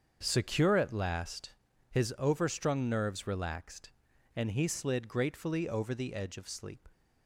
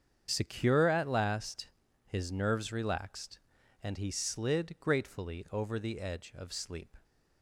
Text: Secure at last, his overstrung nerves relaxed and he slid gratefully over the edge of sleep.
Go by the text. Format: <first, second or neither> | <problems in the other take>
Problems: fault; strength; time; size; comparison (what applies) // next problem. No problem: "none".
first | starts louder than the rest; strong; until 1.3 s; 7.5 dB; also in the first // skips "overstrung"; at 2.3 s